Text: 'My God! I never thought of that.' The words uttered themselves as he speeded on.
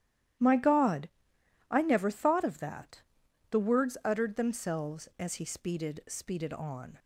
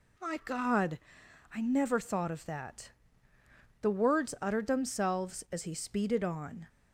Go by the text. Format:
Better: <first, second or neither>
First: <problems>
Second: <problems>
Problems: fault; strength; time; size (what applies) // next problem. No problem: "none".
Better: second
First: starts louder than the rest; strong; until 2.0 s; 12.5 dB // says "speeded" twice; at 6.0 s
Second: none